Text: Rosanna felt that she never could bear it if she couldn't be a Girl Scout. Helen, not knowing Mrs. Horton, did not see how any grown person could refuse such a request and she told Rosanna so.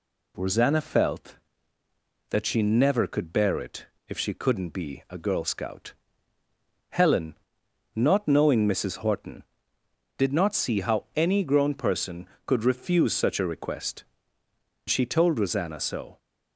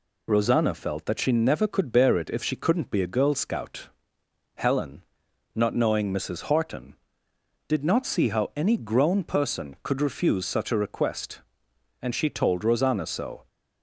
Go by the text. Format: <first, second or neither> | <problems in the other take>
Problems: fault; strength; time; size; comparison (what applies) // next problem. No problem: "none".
second | pauses between "it" and "if"; slight; at 3.8 s; 0.20 s long // skips "and"; at 14.4 s